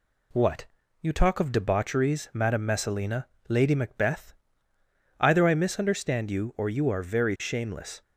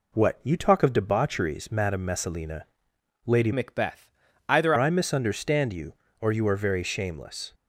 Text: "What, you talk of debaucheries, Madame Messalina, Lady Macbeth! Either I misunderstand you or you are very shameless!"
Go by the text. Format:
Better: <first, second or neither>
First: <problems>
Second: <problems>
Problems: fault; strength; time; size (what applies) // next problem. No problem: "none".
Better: first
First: none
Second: changes voice from "Macbeth" to "Either"; from 3.5 to 4.7 s; 1.2 s long